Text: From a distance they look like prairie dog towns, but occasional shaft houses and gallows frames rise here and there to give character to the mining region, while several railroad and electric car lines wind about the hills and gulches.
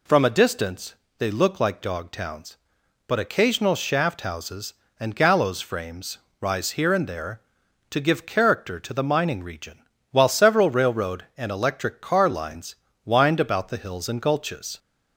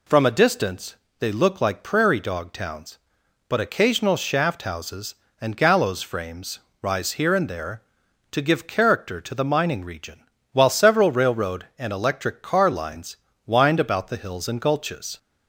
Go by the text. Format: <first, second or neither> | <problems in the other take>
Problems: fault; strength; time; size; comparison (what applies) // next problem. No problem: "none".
second | pauses between "distance" and "they"; slight; at 0.9 s; 0.24 s long; slight in the second // skips "prairie"; at 1.8 s // pauses between "frames" and "rise"; slight; at 6.1 s; 0.22 s long; slight in the second // pauses between "lines" and "wind"; slight; at 12.7 s; 0.28 s long; slight in the second